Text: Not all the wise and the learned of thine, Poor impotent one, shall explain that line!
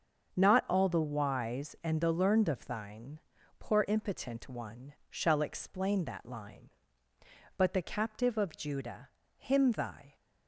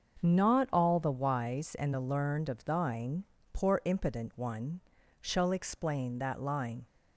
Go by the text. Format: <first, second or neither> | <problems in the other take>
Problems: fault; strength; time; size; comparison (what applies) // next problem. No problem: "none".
second | starts louder than the rest; until 1.4 s; 7 dB; also in the second // goes on to say "But the captive of Judah him thy"; strong; from 7.5 s on; 2.5 s long